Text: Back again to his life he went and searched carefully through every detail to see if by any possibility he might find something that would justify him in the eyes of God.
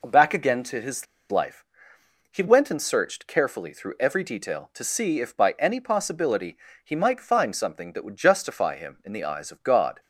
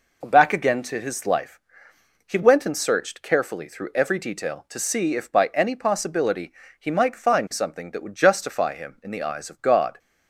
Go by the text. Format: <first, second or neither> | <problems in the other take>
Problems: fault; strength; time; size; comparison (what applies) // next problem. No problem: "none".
second | pauses between "his" and "life"; slight; at 1.0 s; 0.24 s long // pauses between "life" and "he"; noticeable; at 1.6 s; 0.68 s long; noticeable in the second // pauses between "possibility" and "he"; slight; at 6.5 s; 0.28 s long; slight in the second